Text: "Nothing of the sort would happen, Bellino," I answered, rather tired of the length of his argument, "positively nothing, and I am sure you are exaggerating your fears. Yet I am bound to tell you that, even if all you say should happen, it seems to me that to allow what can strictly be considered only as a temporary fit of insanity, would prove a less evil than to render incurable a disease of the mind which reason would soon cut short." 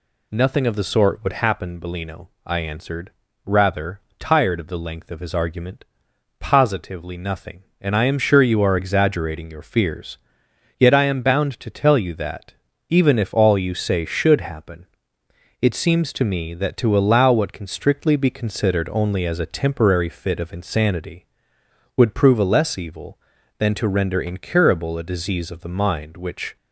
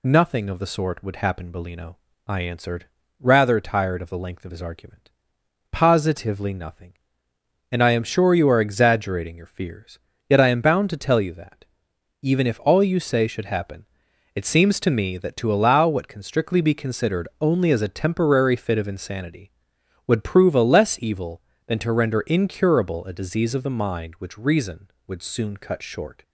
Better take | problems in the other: second | pauses between "rather" and "tired"; slight; at 4.0 s; 0.18 s long // stops before "reason would soon cut short"; at 26.5 s

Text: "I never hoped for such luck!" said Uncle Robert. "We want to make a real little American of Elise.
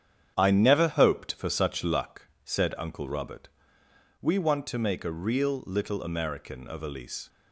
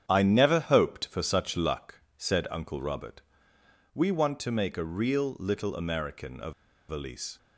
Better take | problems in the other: first | starts louder than the rest; strong; until 1.0 s; 8.5 dB; strong in the first // pauses between "of" and "Elise"; at 6.5 s; 0.37 s long

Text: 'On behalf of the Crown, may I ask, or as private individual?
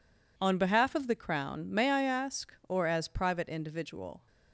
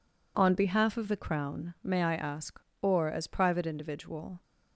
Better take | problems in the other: neither | none

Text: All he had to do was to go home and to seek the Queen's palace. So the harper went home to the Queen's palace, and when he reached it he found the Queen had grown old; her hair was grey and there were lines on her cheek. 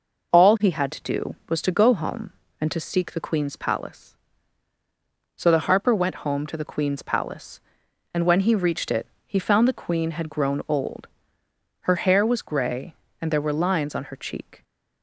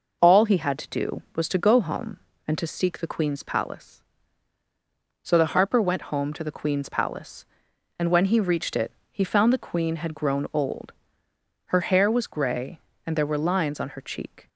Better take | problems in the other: neither | pauses between "it" and "he"; slight; the same in both

